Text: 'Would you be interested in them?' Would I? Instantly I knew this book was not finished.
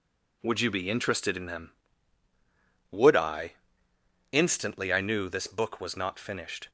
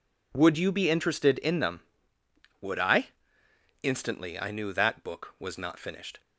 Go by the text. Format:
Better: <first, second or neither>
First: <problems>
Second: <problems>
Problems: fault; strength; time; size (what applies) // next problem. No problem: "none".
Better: first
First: none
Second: says "that" for "this"; at 4.7 s